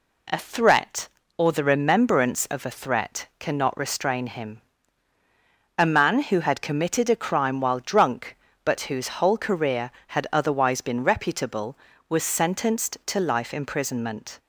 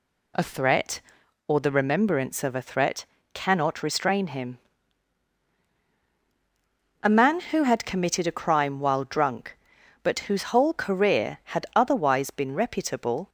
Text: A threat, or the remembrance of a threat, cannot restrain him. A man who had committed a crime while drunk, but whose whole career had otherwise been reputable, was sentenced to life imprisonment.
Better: first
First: none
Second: stops before "was sentenced to life imprisonment"; at 13.2 s

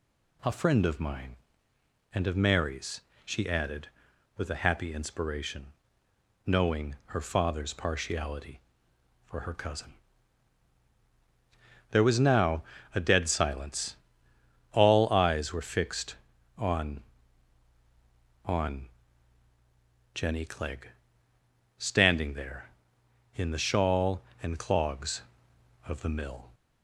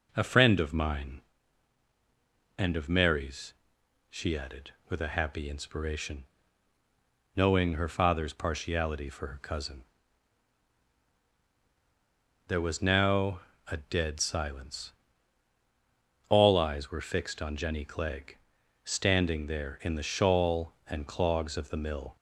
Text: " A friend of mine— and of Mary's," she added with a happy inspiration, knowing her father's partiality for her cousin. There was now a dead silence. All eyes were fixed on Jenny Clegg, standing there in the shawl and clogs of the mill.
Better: second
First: pauses between "now" and "a"; slight; at 12.6 s; 0.32 s long // says "on" twice; at 18.4 s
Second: pauses between "now" and "a"; slight; at 13.4 s; 0.26 s long

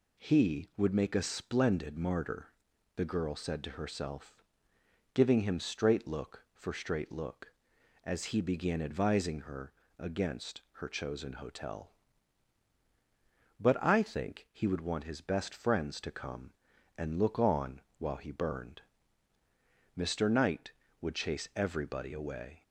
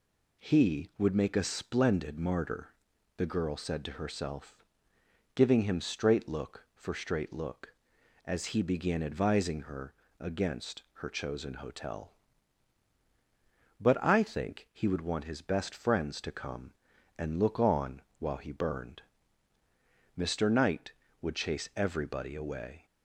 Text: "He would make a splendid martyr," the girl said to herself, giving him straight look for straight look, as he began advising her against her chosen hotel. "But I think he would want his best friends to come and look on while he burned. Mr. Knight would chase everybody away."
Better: neither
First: pauses between "her" and "against"; slight; at 9.7 s; 0.26 s long // pauses between "on" and "while"; slight; at 17.8 s; 0.18 s long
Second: pauses between "her" and "against"; slight; at 9.9 s; 0.26 s long // pauses between "on" and "while"; slight; at 18.0 s; 0.18 s long

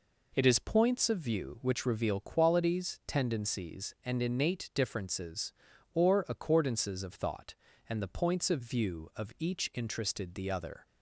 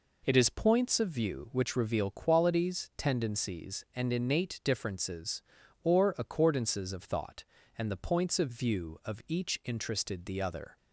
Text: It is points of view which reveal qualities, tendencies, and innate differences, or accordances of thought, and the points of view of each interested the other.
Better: neither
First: none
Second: none

